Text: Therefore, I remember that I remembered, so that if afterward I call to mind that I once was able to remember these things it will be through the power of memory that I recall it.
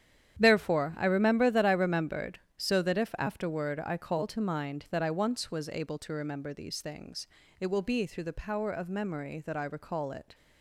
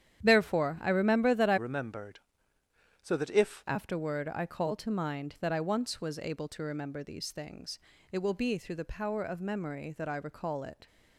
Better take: first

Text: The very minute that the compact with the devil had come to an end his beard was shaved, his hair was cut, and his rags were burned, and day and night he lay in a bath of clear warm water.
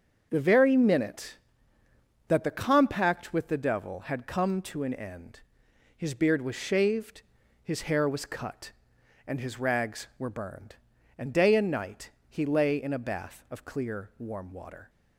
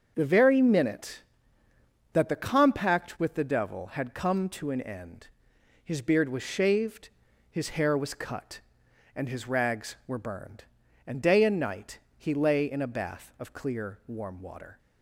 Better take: neither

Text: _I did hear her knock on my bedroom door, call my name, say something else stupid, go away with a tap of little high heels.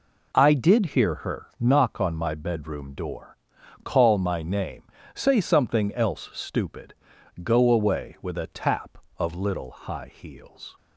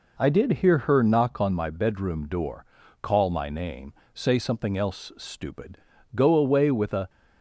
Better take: first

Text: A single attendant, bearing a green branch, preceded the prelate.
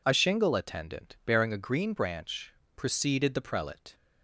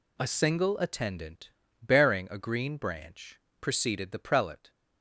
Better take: second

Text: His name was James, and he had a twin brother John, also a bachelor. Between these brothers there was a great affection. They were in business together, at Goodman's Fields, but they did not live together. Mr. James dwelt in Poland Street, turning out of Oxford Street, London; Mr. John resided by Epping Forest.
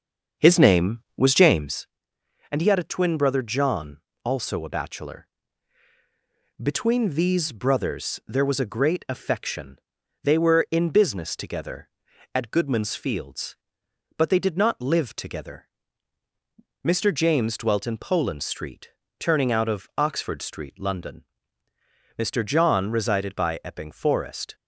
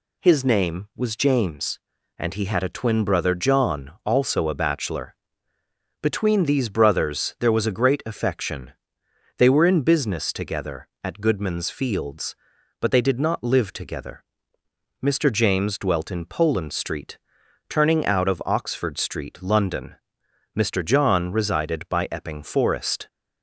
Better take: second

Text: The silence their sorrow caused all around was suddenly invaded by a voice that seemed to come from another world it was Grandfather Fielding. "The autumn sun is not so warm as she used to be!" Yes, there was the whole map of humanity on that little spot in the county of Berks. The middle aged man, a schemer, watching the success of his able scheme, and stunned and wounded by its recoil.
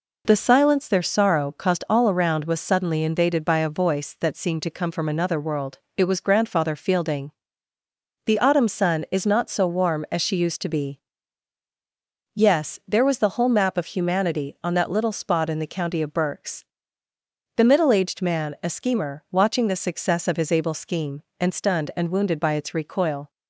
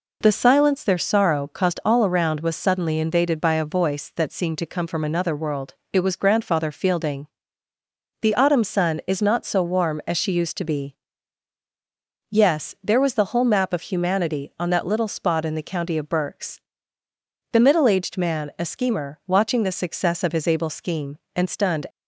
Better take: first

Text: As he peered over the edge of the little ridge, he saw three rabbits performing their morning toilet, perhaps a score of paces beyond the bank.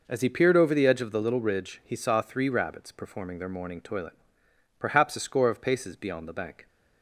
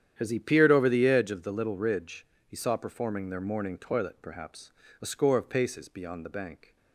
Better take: first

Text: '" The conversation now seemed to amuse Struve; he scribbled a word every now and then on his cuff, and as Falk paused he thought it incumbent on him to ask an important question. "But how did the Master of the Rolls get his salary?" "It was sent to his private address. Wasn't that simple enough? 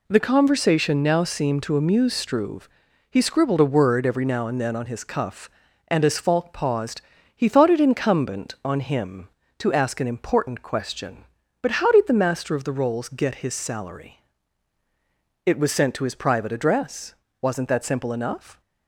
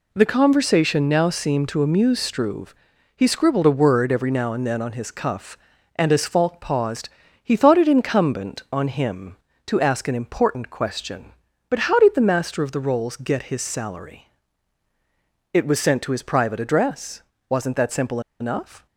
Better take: first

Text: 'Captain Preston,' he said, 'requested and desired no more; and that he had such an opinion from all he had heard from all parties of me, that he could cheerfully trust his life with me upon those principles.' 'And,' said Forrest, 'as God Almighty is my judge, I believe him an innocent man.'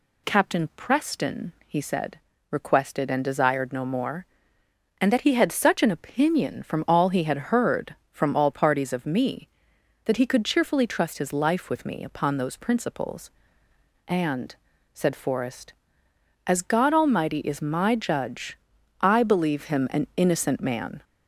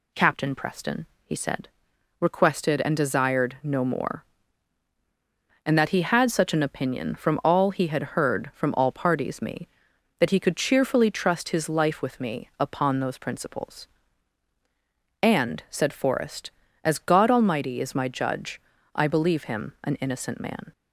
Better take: first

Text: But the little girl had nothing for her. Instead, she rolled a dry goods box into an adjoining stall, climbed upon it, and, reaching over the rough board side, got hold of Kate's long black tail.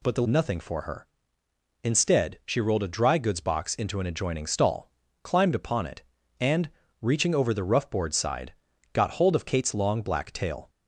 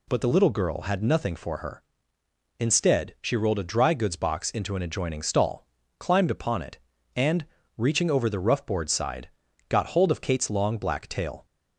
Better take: second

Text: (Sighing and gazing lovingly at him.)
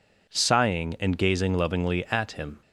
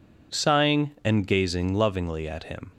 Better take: neither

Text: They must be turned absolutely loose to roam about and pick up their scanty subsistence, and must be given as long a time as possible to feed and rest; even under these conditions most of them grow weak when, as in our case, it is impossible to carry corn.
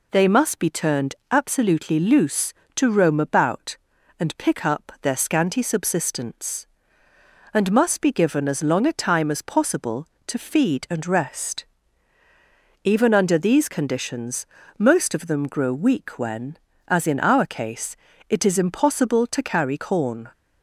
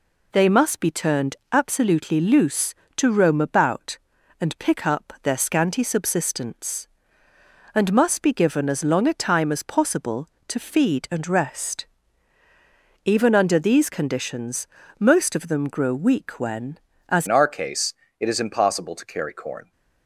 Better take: first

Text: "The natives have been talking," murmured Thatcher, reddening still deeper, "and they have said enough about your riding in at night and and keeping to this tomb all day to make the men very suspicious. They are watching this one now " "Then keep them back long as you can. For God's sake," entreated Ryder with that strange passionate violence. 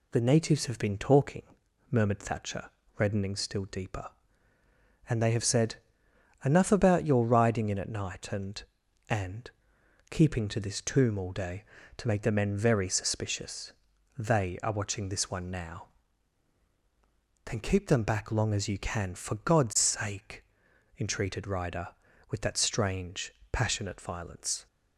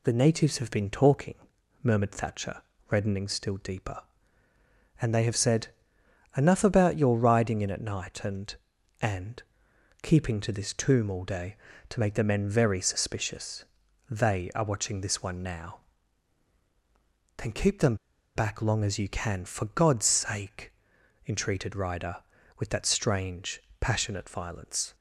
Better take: first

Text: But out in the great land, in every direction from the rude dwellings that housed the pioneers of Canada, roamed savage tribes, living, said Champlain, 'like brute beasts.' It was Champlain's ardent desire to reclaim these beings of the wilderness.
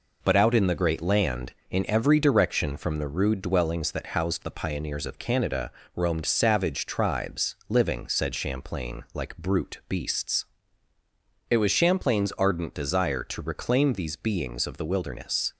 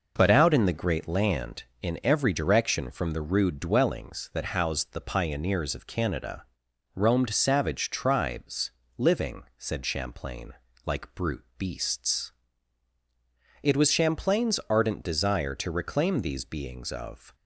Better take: first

